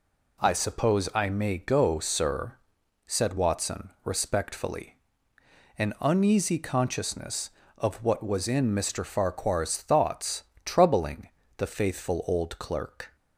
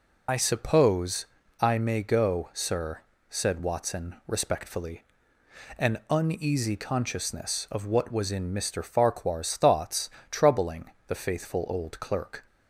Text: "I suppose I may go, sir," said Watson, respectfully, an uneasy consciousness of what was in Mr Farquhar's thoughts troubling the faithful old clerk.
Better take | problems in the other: first | loses the start of "I"; at 0.2 s; 80 ms // pauses between "suppose" and "I"; slight; at 1.2 s; 0.34 s long // pauses between "thoughts" and "troubling"; slight; at 10.0 s; 0.22 s long; slight in the first // pauses between "troubling" and "the"; slight; at 10.8 s; 0.18 s long; slight in the first

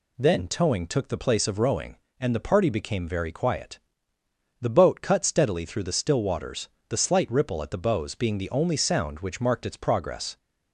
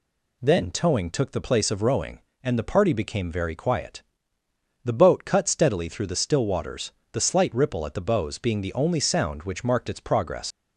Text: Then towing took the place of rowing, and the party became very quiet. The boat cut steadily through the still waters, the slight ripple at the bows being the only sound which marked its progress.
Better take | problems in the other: first | leaves "progress" unfinished; at 10.5 s; 100 ms

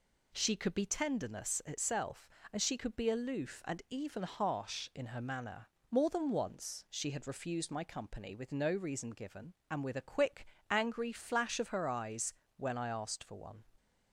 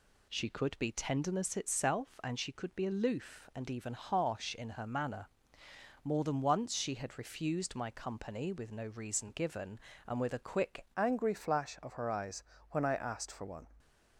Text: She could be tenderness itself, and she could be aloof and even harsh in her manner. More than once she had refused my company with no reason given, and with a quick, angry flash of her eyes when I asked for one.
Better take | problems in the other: first | changes voice at "angry"; from 10.9 s on; 2.7 s long // pauses between "eyes" and "when"; slight; at 12.4 s; 0.28 s long; slight in the first

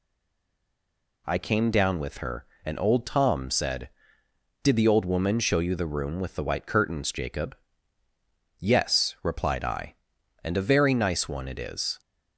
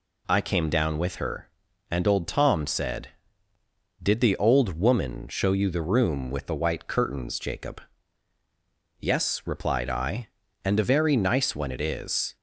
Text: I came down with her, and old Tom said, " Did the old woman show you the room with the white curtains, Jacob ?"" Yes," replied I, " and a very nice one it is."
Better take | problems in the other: second | stays silent before the first word; noticeable; until 1.2 s; 1.2 s long

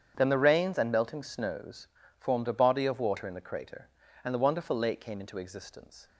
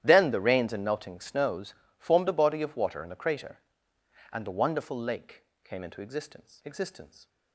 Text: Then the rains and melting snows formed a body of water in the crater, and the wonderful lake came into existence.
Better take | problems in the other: first | starts louder than the rest; strong; until 1.0 s; 11.5 dB; strong in the first // pauses between "snows" and "formed"; slight; at 1.7 s; 0.24 s long; slight in the first // pauses between "lake" and "came"; slight; at 5.4 s; 0.20 s long // says "existence" twice; at 6.6 s

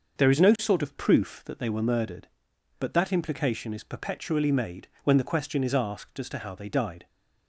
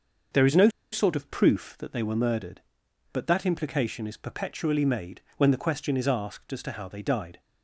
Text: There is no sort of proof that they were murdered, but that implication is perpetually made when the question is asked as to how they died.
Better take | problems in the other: first | starts louder than the rest; until 1.5 s; 6 dB; also in the first // pauses between "no" and "sort"; slight; at 0.6 s; 0.23 s long // pauses between "made" and "when"; slight; at 5.1 s; 0.18 s long; slight in the first

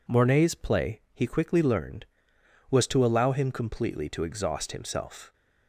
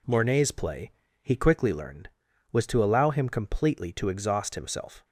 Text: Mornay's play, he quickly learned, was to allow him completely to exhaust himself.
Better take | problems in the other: neither | none

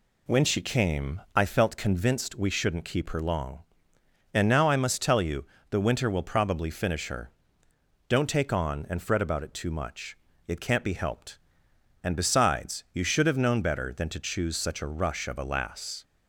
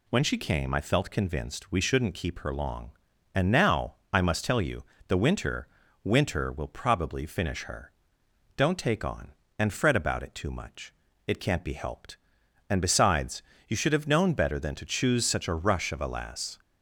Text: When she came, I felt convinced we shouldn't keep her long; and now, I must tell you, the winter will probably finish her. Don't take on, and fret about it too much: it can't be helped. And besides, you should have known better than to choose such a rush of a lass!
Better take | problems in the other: first | says "winter" twice; at 6.0 s

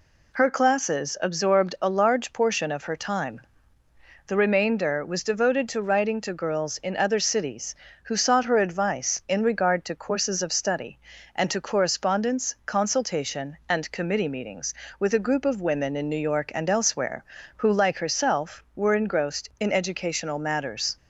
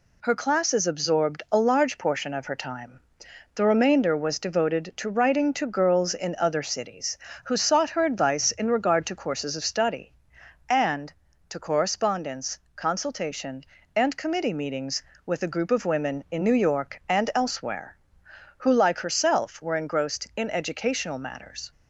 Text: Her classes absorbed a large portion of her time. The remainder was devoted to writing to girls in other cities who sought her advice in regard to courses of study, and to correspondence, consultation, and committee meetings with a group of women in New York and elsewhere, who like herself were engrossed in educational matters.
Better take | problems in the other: neither | none

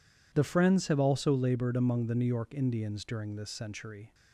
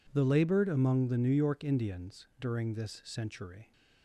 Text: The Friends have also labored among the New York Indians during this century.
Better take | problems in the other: first | skips "Friends have also"; at 0.2 s

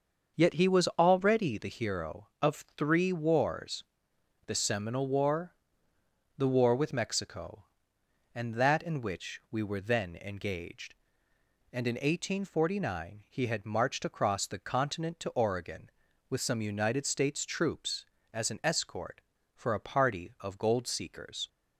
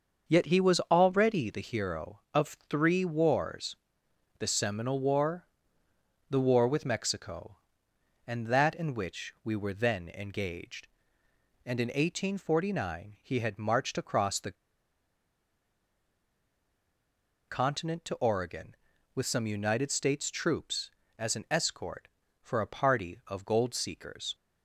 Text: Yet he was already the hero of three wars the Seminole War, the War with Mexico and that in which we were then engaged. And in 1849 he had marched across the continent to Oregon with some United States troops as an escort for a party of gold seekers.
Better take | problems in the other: first | starts louder than the rest; until 1.3 s; 6.5 dB; also in the first // pauses between "wars" and "the"; noticeable; at 3.7 s; 0.62 s long; noticeable in the first // pauses between "the" and "continent"; strong; at 14.5 s; 2.9 s long

